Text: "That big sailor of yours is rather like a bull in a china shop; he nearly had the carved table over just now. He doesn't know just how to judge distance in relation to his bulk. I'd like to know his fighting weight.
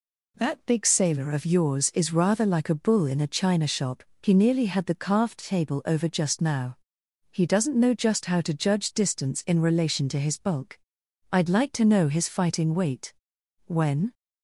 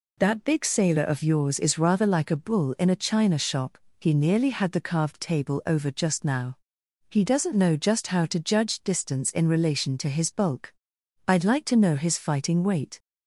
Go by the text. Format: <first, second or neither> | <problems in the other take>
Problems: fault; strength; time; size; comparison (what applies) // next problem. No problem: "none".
second | goes on to say "When"; slight; from 13.6 s on; 0.48 s long